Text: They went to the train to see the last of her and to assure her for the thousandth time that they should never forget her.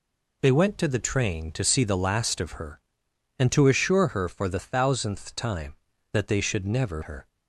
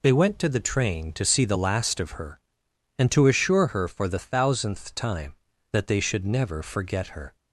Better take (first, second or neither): second